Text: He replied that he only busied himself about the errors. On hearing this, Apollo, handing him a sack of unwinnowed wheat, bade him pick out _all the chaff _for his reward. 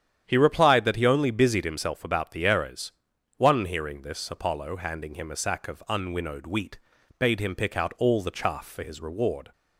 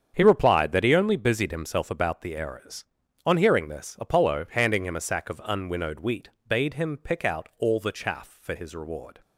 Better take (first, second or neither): second